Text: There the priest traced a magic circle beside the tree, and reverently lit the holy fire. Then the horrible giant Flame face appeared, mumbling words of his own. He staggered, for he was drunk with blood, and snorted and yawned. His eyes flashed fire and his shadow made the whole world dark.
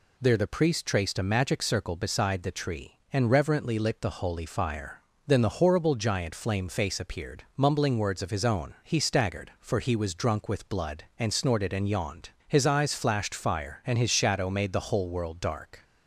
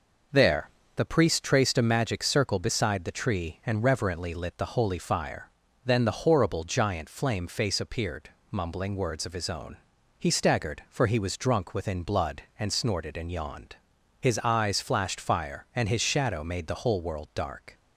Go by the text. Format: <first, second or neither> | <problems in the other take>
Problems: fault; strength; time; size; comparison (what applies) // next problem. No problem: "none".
first | pauses between "There" and "the"; slight; at 0.6 s; 0.26 s long // says "within" for "with"; at 11.7 s